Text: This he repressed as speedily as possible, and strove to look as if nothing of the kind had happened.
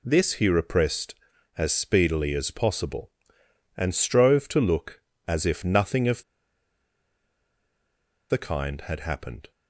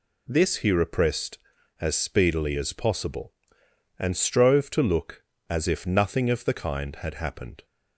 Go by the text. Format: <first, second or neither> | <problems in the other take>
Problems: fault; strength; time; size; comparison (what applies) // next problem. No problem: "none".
second | pauses between "of" and "the"; strong; at 6.2 s; 2.0 s long